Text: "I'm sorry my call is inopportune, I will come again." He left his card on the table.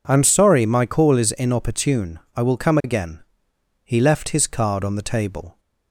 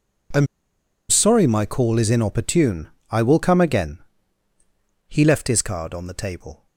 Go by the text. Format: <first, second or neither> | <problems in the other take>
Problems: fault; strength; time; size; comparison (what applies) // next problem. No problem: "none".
first | pauses between "I'm" and "sorry"; noticeable; at 0.4 s; 0.63 s long